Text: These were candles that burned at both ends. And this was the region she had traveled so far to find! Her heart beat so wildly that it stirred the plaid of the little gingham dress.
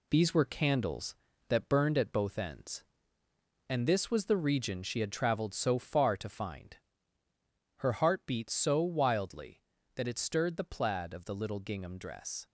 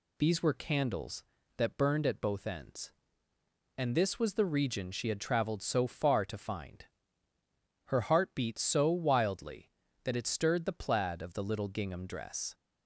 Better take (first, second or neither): second